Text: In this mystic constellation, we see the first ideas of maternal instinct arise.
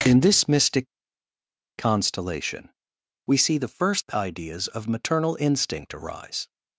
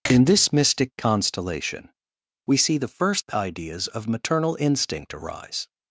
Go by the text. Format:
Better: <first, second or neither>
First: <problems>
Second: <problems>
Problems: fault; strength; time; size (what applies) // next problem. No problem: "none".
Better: second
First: pauses between "mystic" and "constellation"; noticeable; at 0.8 s; 0.89 s long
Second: none